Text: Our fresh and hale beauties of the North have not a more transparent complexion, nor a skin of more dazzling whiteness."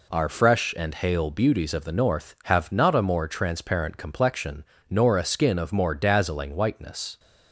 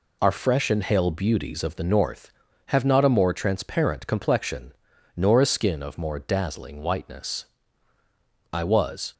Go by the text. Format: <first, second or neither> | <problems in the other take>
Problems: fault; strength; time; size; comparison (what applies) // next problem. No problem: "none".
first | goes on to say "I was"; noticeable; from 8.5 s on; 0.62 s long